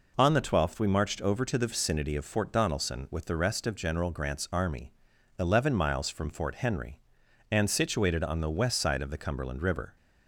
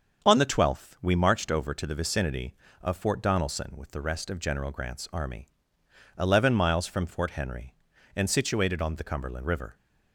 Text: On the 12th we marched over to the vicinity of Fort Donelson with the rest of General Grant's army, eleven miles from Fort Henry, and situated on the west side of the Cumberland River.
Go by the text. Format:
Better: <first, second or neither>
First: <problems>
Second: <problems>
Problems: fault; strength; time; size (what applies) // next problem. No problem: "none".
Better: first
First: none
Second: starts louder than the rest; until 1.3 s; 7 dB // skips "the west side of"; at 8.9 s